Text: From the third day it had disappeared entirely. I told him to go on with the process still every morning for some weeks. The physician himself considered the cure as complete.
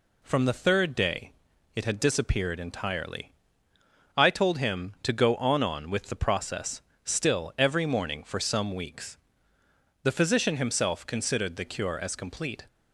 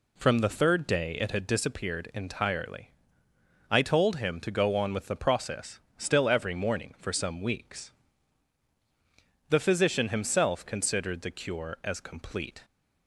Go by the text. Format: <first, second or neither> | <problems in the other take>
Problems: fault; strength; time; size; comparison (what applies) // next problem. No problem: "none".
second | pauses between "day" and "it"; at 1.3 s; 0.44 s long // says "on" twice; at 5.6 s // pauses between "process" and "still"; slight; at 6.8 s; 0.24 s long; slight in the second